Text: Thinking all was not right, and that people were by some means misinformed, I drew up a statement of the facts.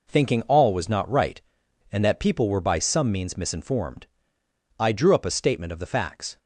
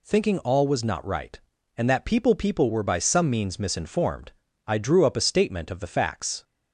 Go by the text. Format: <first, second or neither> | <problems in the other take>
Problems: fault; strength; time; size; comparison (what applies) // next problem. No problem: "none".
first | says "people" twice; at 2.3 s